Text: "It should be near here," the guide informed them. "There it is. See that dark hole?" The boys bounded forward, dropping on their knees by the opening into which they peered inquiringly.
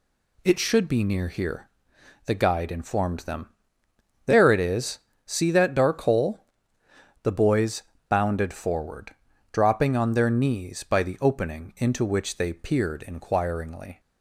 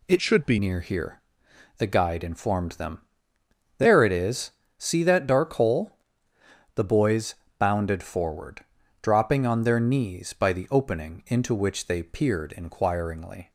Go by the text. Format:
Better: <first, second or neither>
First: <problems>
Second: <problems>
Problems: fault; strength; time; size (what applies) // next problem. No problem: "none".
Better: first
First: pauses between "boys" and "bounded"; slight; at 7.8 s; 0.27 s long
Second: changes voice from "should" to "be"; from 0.1 to 0.5 s; 0.4 s long // pauses between "boys" and "bounded"; slight; at 7.3 s; 0.24 s long